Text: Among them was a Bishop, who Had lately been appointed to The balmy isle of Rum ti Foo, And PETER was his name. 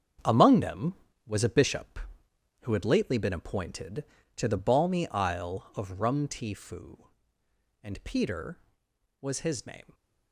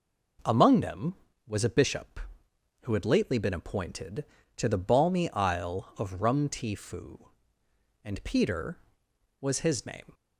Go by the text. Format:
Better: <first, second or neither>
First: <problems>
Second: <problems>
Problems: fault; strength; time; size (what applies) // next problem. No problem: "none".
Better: second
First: gets quieter; strong; throughout; 10.5 dB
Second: none